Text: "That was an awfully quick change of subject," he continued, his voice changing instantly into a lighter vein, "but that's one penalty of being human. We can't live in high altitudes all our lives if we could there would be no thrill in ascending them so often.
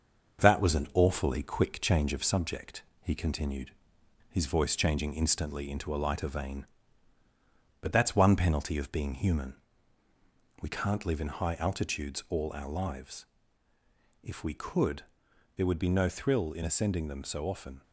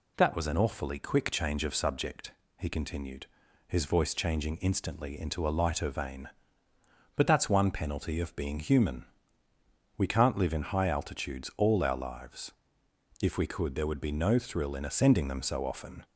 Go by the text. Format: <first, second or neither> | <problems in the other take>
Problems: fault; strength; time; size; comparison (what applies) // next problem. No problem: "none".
second | gets quieter; throughout; 3.5 dB // pauses between "lives" and "if"; noticeable; at 13.2 s; 0.96 s long; noticeable in the second // pauses between "could" and "there"; noticeable; at 15.0 s; 0.52 s long